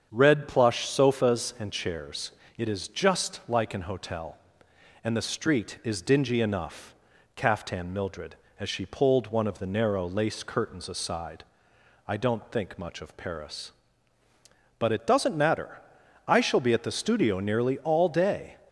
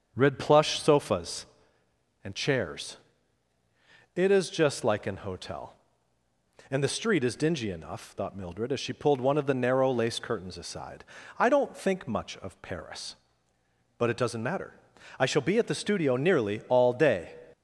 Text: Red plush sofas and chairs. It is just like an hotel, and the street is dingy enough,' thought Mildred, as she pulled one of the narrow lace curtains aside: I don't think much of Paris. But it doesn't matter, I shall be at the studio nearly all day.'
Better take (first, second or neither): second